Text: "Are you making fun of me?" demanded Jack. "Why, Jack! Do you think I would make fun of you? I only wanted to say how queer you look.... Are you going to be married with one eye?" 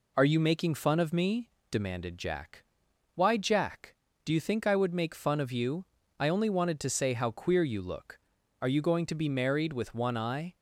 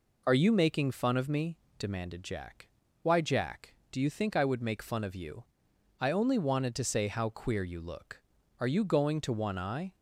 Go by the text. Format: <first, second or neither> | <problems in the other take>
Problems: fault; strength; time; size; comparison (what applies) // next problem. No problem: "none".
first | skips "be married with"; at 9.3 s